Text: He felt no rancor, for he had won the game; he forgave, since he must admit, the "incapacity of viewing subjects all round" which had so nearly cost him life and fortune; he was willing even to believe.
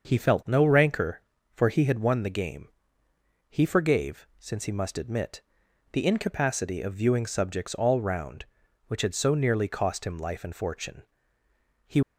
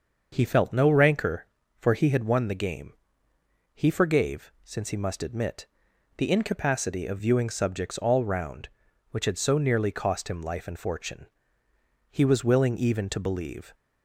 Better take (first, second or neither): second